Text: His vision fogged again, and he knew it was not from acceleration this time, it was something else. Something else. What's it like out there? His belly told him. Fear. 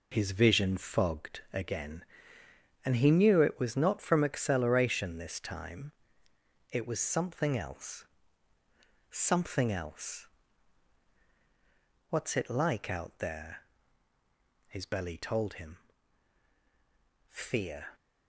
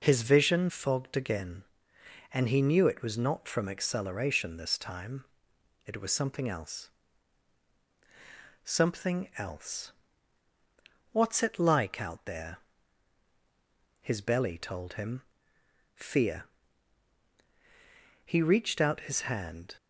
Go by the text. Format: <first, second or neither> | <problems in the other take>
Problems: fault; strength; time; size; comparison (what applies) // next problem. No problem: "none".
first | goes on to say "He reached out his hand"; from 18.2 s on; 1.5 s long